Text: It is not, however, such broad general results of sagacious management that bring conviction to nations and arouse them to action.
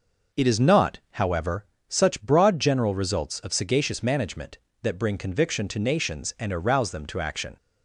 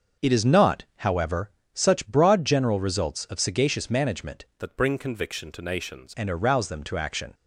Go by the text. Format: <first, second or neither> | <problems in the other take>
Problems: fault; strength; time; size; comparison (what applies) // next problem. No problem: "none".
first | starts louder than the rest; until 1.4 s; 6.5 dB // changes voice from "that" to "nations"; from 4.5 to 6.1 s; 1.6 s long